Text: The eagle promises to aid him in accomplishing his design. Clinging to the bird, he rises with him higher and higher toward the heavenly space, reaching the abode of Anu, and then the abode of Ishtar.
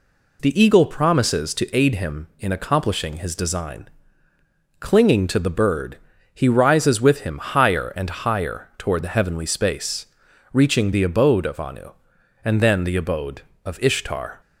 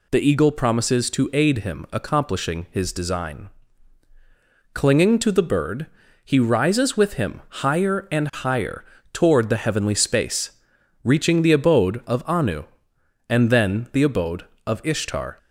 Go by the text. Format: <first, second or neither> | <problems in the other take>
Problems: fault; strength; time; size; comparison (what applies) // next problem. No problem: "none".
first | skips "in"; at 1.8 s // pauses between "higher" and "toward"; slight; at 8.8 s; 0.30 s long